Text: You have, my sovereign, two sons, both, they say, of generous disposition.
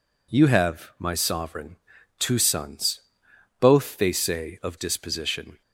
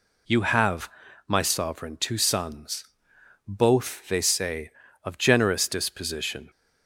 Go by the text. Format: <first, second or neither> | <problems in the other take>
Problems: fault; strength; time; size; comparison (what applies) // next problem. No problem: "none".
second | skips "generous"; at 4.7 s